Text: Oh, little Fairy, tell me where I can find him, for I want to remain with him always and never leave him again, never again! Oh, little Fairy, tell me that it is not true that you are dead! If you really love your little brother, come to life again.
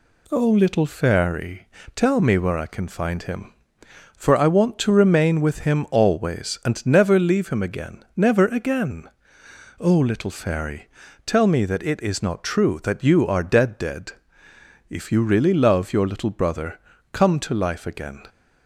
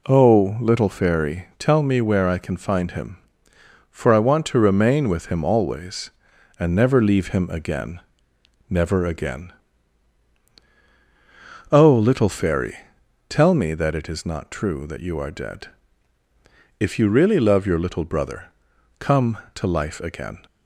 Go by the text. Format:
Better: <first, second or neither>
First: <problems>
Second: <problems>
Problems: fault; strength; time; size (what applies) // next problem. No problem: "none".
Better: second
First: says "dead" twice; at 13.7 s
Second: none